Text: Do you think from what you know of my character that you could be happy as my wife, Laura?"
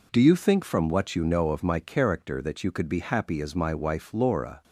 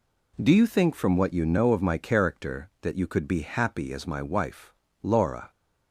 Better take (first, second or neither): neither